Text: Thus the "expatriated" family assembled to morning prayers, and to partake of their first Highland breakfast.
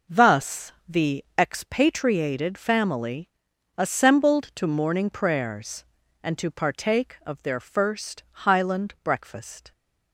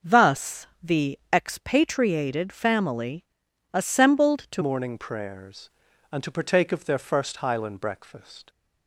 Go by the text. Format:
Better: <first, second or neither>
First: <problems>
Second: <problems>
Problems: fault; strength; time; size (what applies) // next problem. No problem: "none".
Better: first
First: pauses between "Thus" and "the"; slight; at 0.7 s; 0.16 s long // pauses between "family" and "assembled"; noticeable; at 3.2 s; 0.48 s long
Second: pauses between "Thus" and "the"; slight; at 0.6 s; 0.16 s long // pauses between "family" and "assembled"; noticeable; at 3.2 s; 0.48 s long // changes voice at "morning"; from 4.6 s on; 3.8 s long